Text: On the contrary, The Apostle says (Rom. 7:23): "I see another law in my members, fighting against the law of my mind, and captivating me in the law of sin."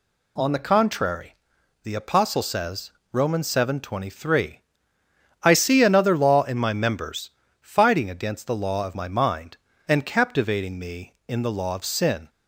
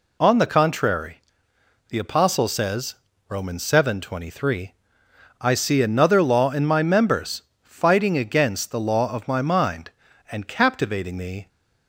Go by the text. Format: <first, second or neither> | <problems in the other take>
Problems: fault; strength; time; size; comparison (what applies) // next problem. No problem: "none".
first | stops before "in the law of sin"; at 11.4 s